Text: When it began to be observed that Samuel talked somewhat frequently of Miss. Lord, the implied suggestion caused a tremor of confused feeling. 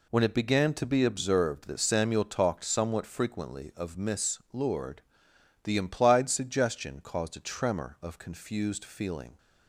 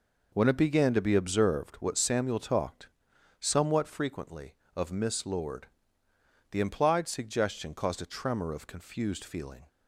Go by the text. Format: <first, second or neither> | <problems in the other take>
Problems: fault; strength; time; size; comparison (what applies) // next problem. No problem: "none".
first | says "what" for "that"; at 1.7 s // pauses between "talked" and "somewhat"; noticeable; at 2.8 s; 0.52 s long